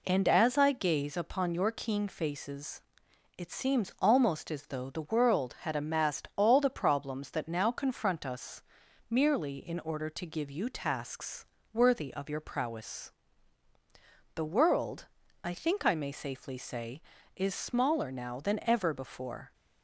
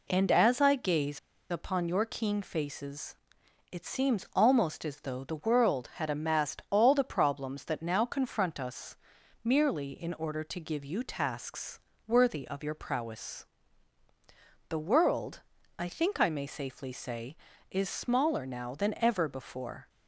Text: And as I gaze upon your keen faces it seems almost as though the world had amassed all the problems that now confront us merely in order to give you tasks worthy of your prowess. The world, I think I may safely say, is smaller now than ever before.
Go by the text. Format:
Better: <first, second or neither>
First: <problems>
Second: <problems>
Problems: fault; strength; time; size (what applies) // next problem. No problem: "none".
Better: first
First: pauses between "faces" and "it"; noticeable; at 2.8 s; 0.56 s long // pauses between "us" and "merely"; noticeable; at 8.6 s; 0.48 s long // pauses between "tasks" and "worthy"; slight; at 11.4 s; 0.28 s long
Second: pauses between "gaze" and "upon"; slight; at 1.1 s; 0.31 s long // pauses between "faces" and "it"; noticeable; at 3.1 s; 0.56 s long // pauses between "us" and "merely"; noticeable; at 8.9 s; 0.48 s long // pauses between "tasks" and "worthy"; slight; at 11.7 s; 0.28 s long